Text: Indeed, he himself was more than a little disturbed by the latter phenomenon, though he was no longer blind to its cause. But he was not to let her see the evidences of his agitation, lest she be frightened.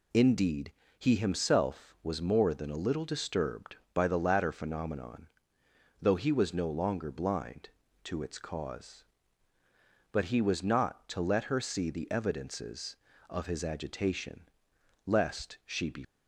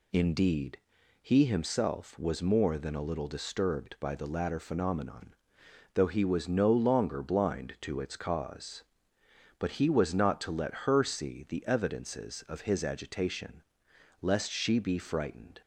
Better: second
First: stops before "frightened"; at 16.0 s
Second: none

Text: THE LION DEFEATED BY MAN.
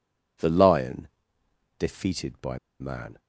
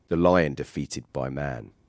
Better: second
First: pauses between "LION" and "DEFEATED"; noticeable; at 1.0 s; 0.72 s long // pauses between "BY" and "MAN"; slight; at 2.5 s; 0.22 s long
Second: none

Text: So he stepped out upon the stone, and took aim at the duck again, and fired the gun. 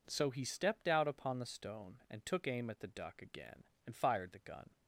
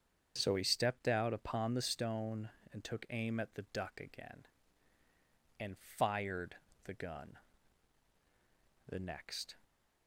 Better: first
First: none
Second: starts louder than the rest; until 1.3 s; 7 dB // pauses between "and" and "fired"; slight; at 5.7 s; 0.22 s long // pauses between "fired" and "the"; slight; at 6.5 s; 0.26 s long // goes on to say "The next"; noticeable; from 8.9 s on; 0.64 s long

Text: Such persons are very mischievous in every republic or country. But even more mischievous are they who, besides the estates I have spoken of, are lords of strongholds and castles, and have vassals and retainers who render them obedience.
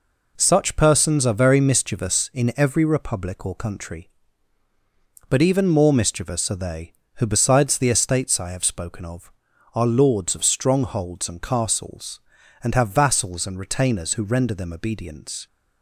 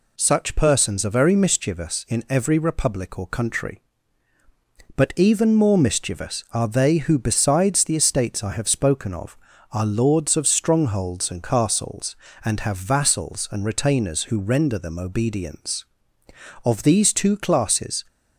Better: first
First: none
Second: goes on to say "Of these two classes"; from 16.6 s on; 1.3 s long

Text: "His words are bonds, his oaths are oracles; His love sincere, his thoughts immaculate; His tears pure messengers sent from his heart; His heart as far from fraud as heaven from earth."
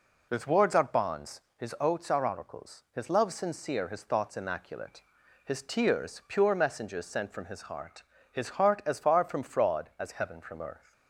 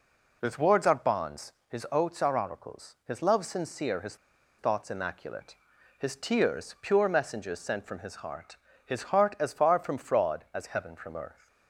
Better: first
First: none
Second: pauses between "his" and "thoughts"; at 4.1 s; 0.42 s long

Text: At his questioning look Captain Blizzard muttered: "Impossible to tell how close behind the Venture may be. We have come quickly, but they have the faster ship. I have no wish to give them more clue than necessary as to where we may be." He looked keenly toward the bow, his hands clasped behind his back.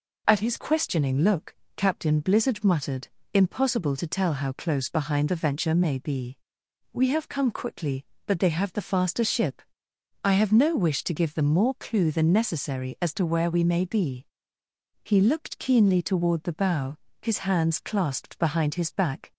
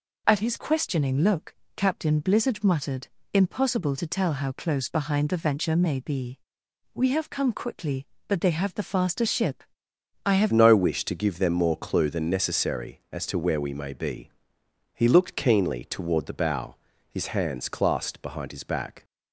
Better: first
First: pauses between "look" and "Captain"; slight; at 1.5 s; 0.20 s long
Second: pauses between "look" and "Captain"; slight; at 1.5 s; 0.20 s long // changes voice at "no"; from 10.4 s on; 8.6 s long

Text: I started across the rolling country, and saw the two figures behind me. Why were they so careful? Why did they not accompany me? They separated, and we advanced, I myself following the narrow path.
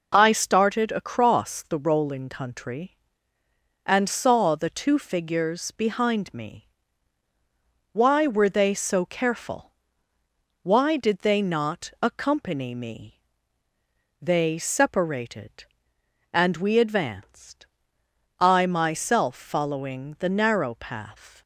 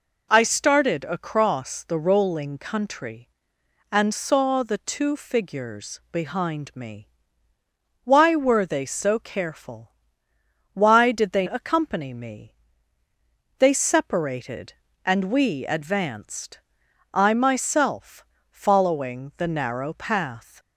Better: first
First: none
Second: skips "not"; at 11.4 s // pauses between "myself" and "following"; slight; at 18.2 s; 0.28 s long

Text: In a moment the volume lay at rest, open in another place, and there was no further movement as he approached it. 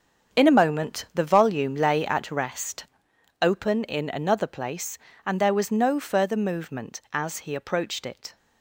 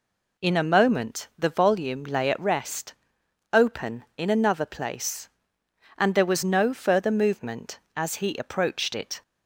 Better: second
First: gets quieter; strong; throughout; 10 dB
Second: none

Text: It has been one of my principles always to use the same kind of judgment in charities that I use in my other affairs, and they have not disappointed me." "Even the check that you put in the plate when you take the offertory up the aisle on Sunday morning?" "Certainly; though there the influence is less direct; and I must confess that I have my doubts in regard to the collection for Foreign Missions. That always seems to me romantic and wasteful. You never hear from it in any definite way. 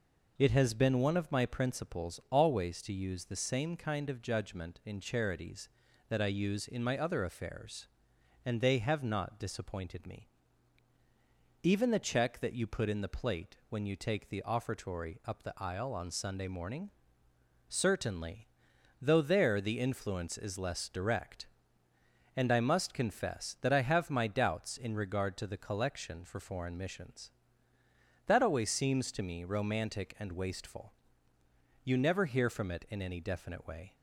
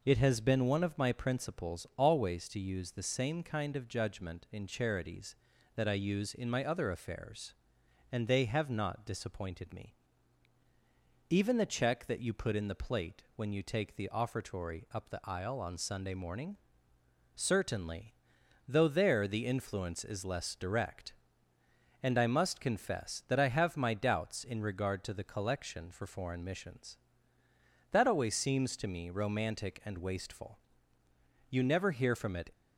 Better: first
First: none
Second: stops before "in any definite way"; at 32.5 s

